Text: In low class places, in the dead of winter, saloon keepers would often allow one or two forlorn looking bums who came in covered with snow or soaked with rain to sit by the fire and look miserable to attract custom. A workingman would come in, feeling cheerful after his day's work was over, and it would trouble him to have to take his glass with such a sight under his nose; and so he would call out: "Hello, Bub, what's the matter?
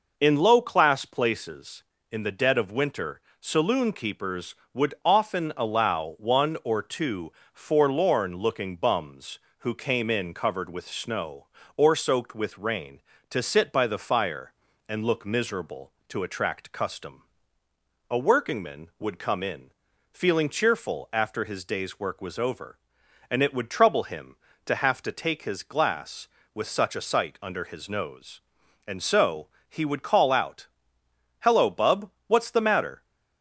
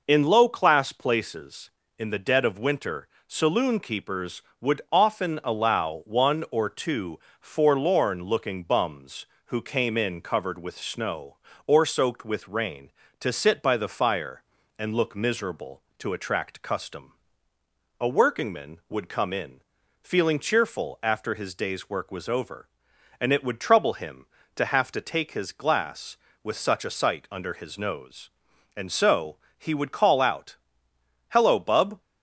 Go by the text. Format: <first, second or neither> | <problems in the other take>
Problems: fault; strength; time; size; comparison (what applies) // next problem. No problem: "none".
first | pauses between "two" and "forlorn"; slight; at 7.1 s; 0.20 s long; slight in the first // pauses between "so" and "he"; slight; at 29.3 s; 0.20 s long; slight in the first // stops before "what's the matter"; at 32.0 s